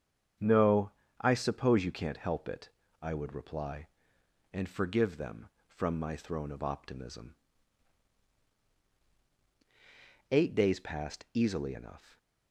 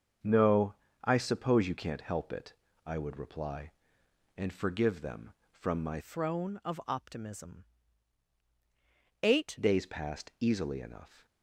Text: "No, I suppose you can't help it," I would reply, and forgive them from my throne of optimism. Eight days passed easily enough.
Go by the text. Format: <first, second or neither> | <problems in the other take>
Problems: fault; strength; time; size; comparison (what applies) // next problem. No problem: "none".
first | starts louder than the rest; until 1.5 s; 6.5 dB; strong in the first // changes voice from "throne" to "Eight"; from 6.0 to 9.5 s; 3.5 s long